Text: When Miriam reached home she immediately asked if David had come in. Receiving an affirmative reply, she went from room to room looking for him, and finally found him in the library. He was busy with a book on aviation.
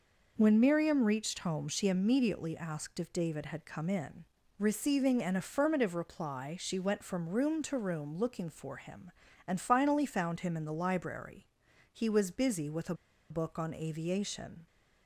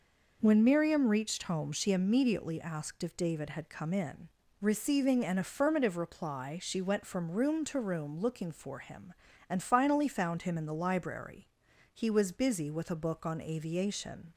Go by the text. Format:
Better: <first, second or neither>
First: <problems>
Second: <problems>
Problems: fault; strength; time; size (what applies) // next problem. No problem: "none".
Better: second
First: pauses between "a" and "book"; slight; at 12.9 s; 0.35 s long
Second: none